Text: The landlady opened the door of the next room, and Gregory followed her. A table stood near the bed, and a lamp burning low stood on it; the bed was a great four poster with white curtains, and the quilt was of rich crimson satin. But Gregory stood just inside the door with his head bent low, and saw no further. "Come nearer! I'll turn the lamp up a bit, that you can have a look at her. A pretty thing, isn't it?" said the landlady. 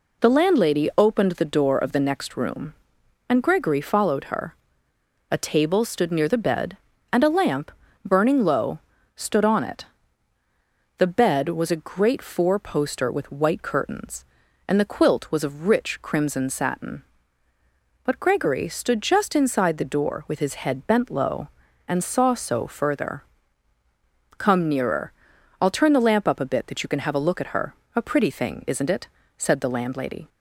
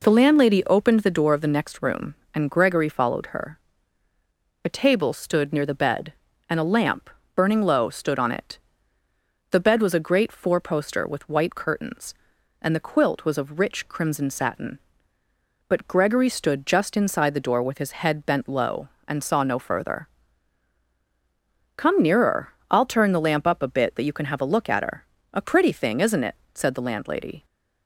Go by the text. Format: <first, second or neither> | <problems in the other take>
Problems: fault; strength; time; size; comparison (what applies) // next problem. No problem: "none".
second | pauses between "lamp" and "burning"; slight; at 7.7 s; 0.32 s long; slight in the second // pauses between "low" and "stood"; slight; at 8.7 s; 0.36 s long // says "so" for "no"; at 22.3 s